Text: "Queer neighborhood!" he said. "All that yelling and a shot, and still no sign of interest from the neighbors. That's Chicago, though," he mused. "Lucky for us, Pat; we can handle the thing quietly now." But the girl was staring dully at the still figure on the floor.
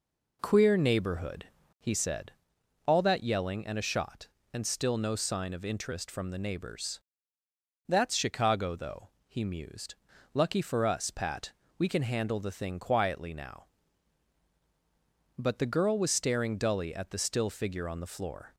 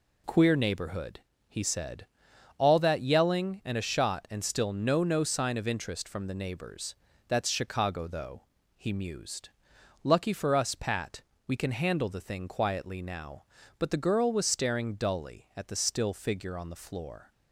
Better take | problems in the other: first | says "no" twice; at 5.0 s

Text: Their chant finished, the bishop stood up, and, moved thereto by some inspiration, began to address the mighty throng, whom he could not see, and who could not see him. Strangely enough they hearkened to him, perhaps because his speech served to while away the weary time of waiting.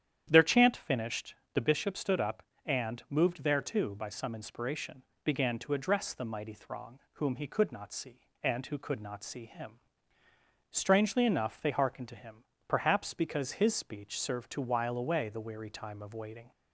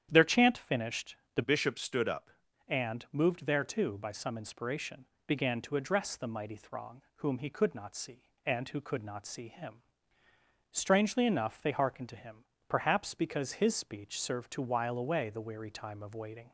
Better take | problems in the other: first | starts louder than the rest; strong; until 1.1 s; 9.5 dB; strong in the first // changes voice from "bishop" to "up"; from 1.4 to 2.2 s; 0.8 s long

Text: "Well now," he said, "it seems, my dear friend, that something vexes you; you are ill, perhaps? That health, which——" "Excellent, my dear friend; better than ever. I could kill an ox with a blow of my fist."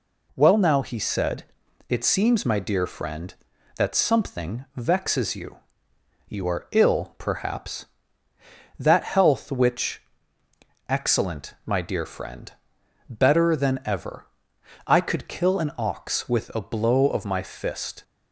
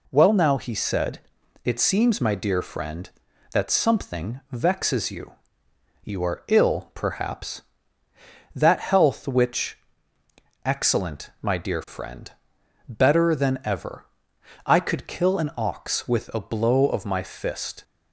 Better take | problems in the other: neither | none

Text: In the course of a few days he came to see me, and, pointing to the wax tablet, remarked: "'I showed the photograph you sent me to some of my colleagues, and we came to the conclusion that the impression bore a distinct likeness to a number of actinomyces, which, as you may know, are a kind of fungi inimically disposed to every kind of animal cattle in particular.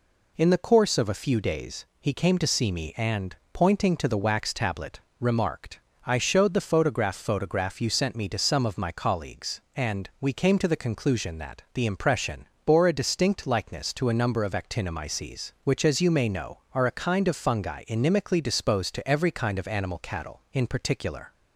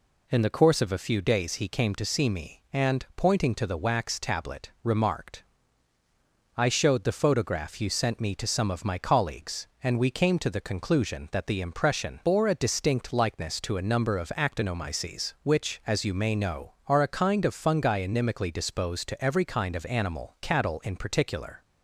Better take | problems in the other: second | says "photograph" twice; at 7.1 s // pauses between "impression" and "bore"; slight; at 12.4 s; 0.18 s long

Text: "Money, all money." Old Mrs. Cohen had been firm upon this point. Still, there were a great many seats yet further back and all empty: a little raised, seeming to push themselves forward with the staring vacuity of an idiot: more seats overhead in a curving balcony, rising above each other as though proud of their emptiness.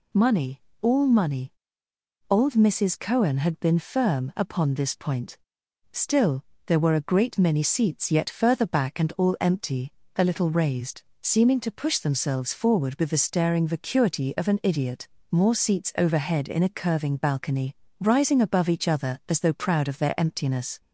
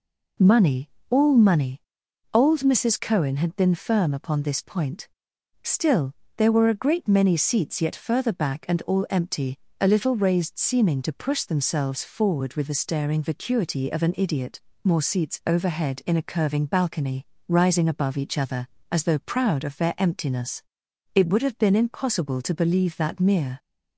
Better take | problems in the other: first | goes on to say "It would have been impossible to believe that mere"; strong; from 21.1 s on; 2.4 s long

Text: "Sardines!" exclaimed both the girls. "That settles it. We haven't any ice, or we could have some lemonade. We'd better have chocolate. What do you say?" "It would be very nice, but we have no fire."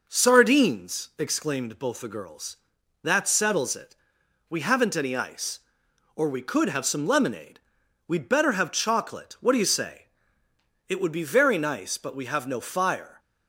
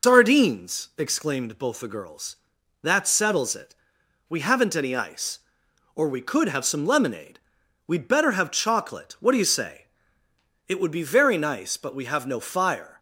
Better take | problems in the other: first | loses the start of "Sardines"; at 0.0 s; 145 ms

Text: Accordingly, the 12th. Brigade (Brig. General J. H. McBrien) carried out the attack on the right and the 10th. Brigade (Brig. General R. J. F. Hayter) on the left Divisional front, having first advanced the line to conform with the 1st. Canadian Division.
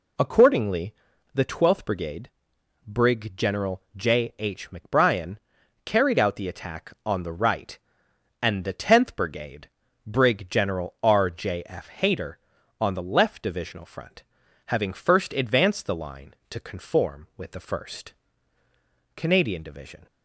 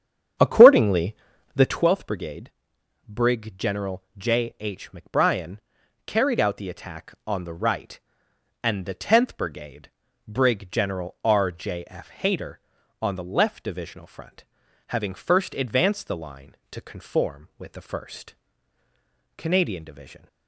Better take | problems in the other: first | starts louder than the rest; strong; until 1.9 s; 8.5 dB // pauses between "General" and "J"; slight; at 4.0 s; 0.16 s long; slight in the first

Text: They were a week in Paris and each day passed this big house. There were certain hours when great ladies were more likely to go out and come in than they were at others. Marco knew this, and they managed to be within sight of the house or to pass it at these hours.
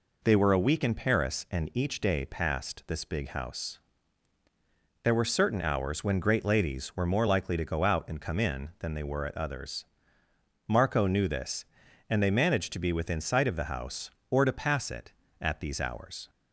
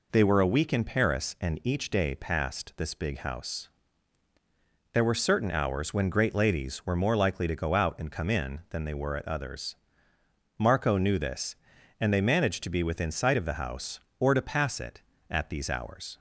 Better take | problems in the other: neither | none

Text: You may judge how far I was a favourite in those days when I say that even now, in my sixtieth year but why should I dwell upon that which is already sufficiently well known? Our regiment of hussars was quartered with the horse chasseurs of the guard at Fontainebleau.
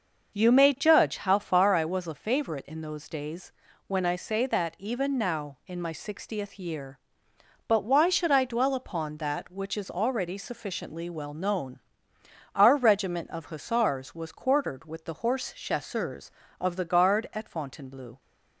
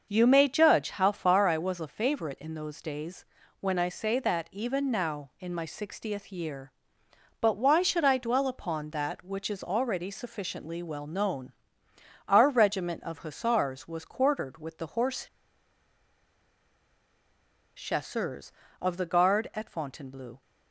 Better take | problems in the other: first | starts louder than the rest; until 1.1 s; 6 dB; also in the first // pauses between "days" and "when"; slight; at 3.2 s; 0.36 s long; slight in the first // pauses between "horse" and "chasseurs"; strong; at 15.2 s; 2.4 s long

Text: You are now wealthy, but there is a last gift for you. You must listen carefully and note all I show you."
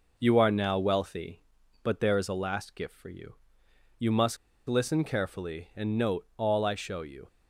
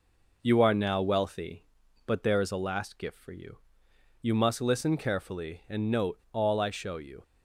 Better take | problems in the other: second | pauses between "must" and "listen"; slight; at 4.3 s; 0.32 s long

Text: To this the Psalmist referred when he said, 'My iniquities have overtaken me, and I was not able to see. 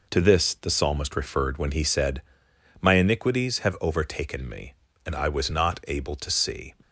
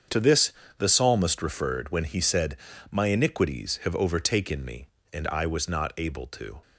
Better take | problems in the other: first | starts louder than the rest; strong; until 1.3 s; 7.5 dB // pauses between "this" and "the"; slight; at 0.5 s; 0.28 s long // stops before "see"; at 6.6 s

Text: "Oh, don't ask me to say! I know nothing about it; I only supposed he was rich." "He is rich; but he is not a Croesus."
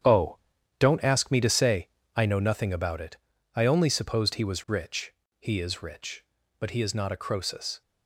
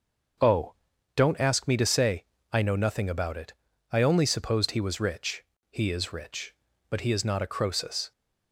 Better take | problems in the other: second | gets quieter; strong; throughout; 9.5 dB // starts louder than the rest; strong; until 1.4 s; 8.5 dB; noticeable in the second

